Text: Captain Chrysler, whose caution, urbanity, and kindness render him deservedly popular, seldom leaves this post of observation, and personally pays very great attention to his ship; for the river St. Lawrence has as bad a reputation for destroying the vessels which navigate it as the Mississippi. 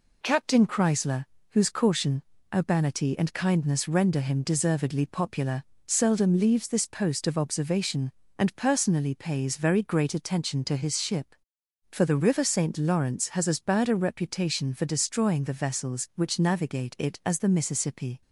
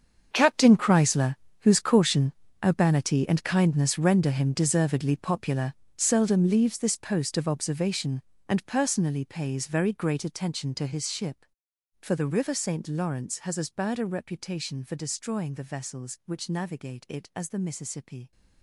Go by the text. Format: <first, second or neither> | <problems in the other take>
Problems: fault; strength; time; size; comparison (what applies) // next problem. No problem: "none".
first | gets quieter; strong; throughout; 15 dB